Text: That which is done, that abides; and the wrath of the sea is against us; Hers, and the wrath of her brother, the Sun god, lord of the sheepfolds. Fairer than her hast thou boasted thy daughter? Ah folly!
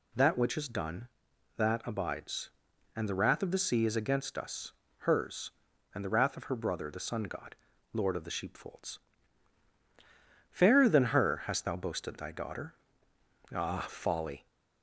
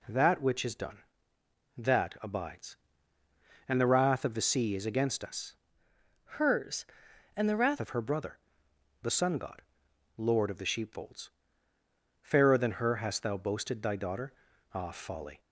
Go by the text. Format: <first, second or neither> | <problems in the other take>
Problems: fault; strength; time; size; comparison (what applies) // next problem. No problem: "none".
first | changes voice from "Hers" to "wrath"; from 6.2 to 7.7 s; 1.5 s long